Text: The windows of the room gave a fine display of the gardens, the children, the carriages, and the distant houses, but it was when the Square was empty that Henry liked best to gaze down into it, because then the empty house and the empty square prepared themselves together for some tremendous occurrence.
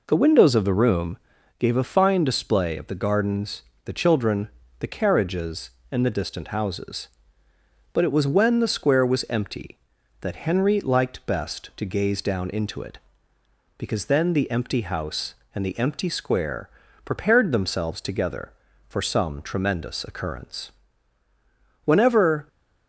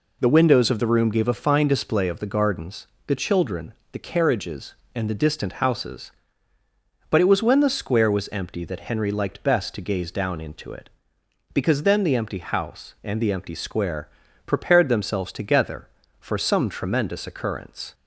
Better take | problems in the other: second | pauses between "room" and "gave"; at 1.1 s; 0.42 s long // pauses between "square" and "prepared"; slight; at 16.6 s; 0.36 s long; also in the second // goes on to say "Whenever"; noticeable; from 21.8 s on; 0.62 s long

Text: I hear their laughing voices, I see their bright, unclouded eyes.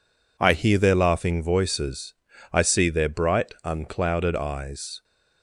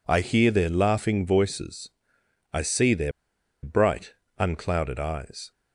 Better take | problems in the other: first | pauses between "their" and "bright"; noticeable; at 3.1 s; 0.53 s long

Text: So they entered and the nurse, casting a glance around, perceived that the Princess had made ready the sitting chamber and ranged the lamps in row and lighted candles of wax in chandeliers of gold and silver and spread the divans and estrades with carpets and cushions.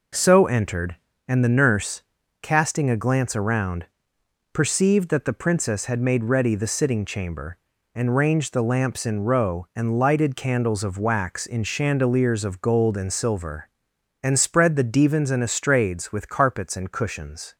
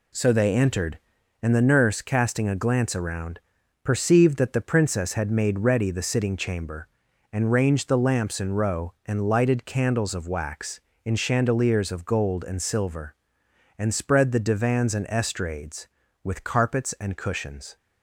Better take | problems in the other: second | skips "they"; at 0.4 s

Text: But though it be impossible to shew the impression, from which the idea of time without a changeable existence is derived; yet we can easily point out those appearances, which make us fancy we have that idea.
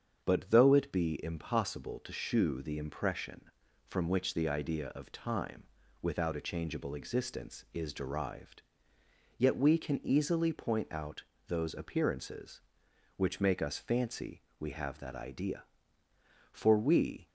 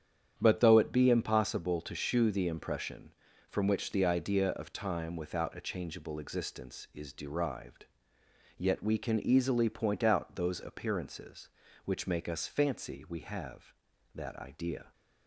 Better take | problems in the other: second | starts louder than the rest; strong; until 1.2 s; 7.5 dB; strong in the second // pauses between "time" and "without"; slight; at 5.6 s; 0.36 s long // pauses between "out" and "those"; slight; at 11.2 s; 0.24 s long // pauses between "fancy" and "we"; slight; at 14.4 s; 0.18 s long // goes on to say "For we"; noticeable; from 16.5 s on; 0.74 s long

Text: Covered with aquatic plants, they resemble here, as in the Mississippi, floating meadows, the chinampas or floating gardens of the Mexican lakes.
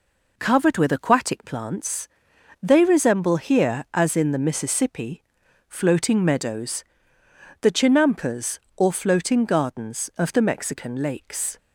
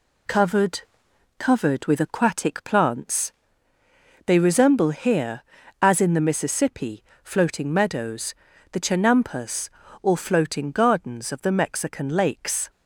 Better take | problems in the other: first | says "Covered" twice; at 1.3 s

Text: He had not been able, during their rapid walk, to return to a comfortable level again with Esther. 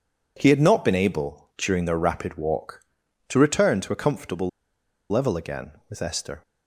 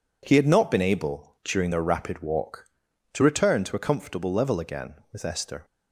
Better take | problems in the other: second | pauses between "comfortable" and "level"; noticeable; at 4.4 s; 0.62 s long

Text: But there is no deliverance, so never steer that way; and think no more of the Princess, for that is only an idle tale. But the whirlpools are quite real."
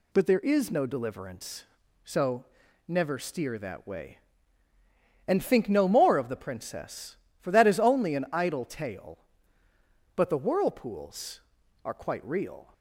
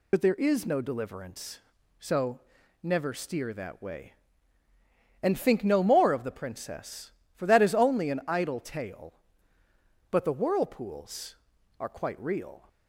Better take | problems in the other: first | loses the start of "But"; at 0.1 s; 55 ms // pauses between "so" and "never"; at 2.3 s; 0.42 s long; also in the first

